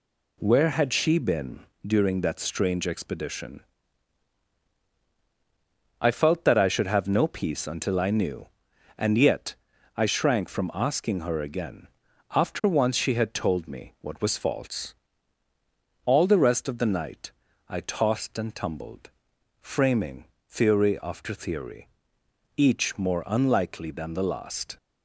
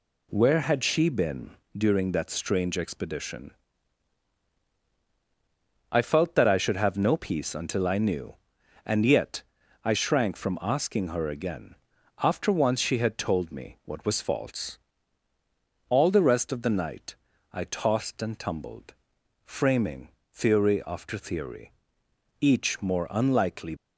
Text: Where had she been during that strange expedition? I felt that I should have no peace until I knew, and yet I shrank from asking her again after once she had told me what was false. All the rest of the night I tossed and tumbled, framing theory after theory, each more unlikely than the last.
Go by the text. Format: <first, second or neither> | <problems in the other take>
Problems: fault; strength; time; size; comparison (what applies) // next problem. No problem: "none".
first | pauses between "been" and "during"; slight; at 1.5 s; 0.20 s long; slight in the first // pauses between "yet" and "I"; at 9.4 s; 0.42 s long; also in the first // pauses between "again" and "after"; at 11.7 s; 0.44 s long; also in the first // pauses between "night" and "I"; at 17.1 s; 0.38 s long; also in the first // pauses between "framing" and "theory"; slight; at 20.0 s; 0.24 s long; slight in the first // stops before "than the last"; at 23.7 s